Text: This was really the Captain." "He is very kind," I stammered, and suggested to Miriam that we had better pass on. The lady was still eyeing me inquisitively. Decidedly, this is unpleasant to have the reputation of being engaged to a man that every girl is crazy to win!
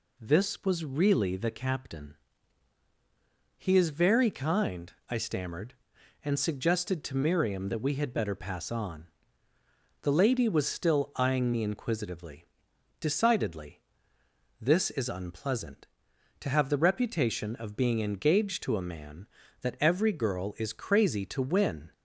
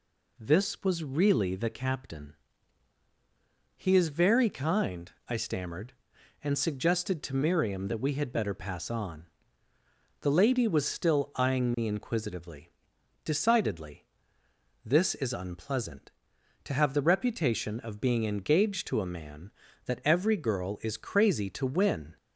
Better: neither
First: none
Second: none

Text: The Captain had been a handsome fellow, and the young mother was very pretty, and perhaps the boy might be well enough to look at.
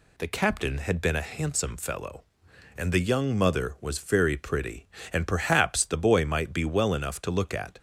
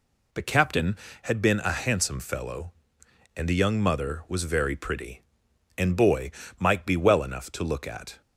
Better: first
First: none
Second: skips "perhaps the"; at 5.9 s // pauses between "boy" and "might"; slight; at 6.3 s; 0.26 s long

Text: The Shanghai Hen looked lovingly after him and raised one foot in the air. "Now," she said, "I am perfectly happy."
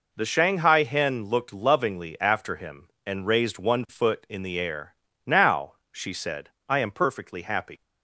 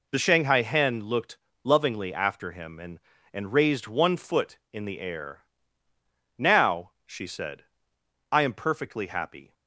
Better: first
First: none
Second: pauses between "looked" and "lovingly"; slight; at 1.3 s; 0.28 s long // says "and" twice; at 3.3 s

